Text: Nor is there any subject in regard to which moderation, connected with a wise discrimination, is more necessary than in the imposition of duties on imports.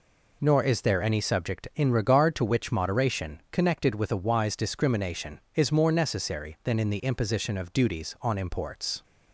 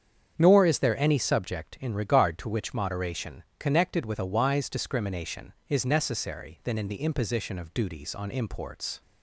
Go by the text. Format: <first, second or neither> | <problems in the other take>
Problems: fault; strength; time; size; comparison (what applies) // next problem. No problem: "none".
first | starts louder than the rest; strong; until 1.3 s; 8 dB // skips "more"; at 5.8 s